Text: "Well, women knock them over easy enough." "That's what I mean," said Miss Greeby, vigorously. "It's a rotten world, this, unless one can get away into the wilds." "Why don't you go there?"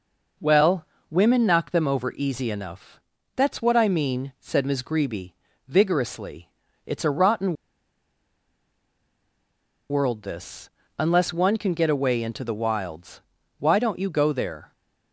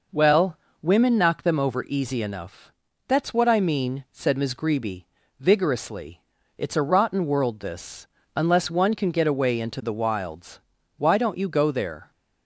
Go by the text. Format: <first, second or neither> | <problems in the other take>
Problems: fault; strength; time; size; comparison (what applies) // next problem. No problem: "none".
second | pauses between "rotten" and "world"; strong; at 7.5 s; 2.3 s long